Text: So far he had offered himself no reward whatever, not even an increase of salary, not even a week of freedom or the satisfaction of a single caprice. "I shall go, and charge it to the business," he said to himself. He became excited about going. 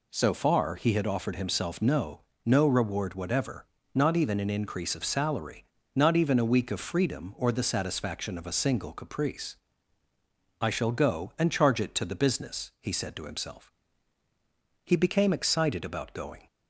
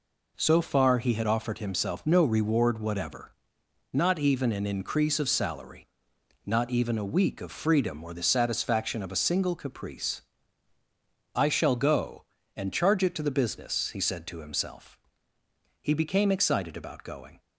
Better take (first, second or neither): second